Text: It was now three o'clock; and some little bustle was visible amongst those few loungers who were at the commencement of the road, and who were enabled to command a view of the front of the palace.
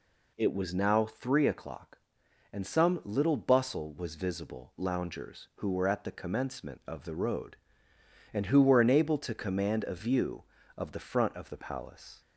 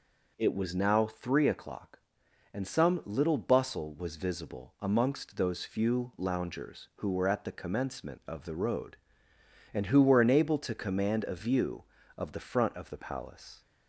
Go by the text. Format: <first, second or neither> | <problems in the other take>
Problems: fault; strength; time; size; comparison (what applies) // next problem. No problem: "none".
second | skips "amongst those few"; at 4.7 s